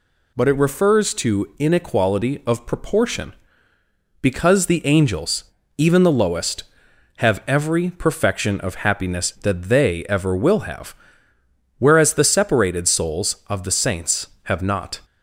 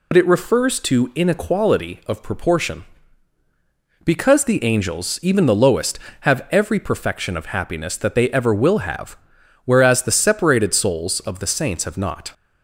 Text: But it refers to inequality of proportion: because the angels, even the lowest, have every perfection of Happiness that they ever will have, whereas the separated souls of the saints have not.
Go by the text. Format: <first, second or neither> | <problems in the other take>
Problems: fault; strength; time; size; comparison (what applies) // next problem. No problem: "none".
first | loses the start of "But"; at 0.1 s; 60 ms